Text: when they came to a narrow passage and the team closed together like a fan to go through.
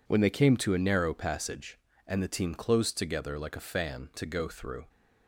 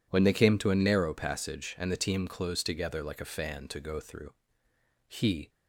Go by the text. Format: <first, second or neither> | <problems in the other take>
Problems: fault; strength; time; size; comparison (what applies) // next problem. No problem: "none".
first | goes on to say "He"; slight; from 5.0 s on; 0.42 s long